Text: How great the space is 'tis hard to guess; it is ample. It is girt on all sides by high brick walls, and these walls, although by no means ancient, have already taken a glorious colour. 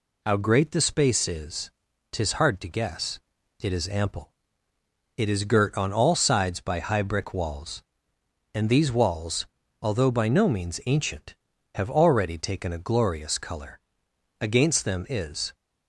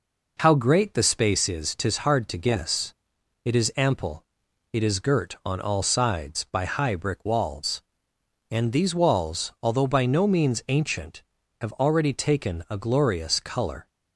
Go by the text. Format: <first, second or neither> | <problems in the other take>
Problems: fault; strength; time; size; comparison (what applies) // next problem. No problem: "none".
second | pauses between "is" and "tis"; at 1.7 s; 0.40 s long // goes on to say "Against them is"; noticeable; from 14.4 s on; 1.1 s long